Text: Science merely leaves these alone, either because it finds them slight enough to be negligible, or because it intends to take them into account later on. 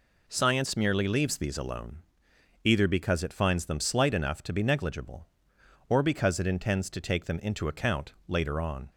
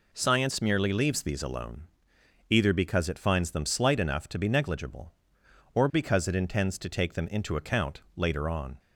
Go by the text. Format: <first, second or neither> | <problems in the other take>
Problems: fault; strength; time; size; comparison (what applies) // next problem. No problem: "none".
neither | none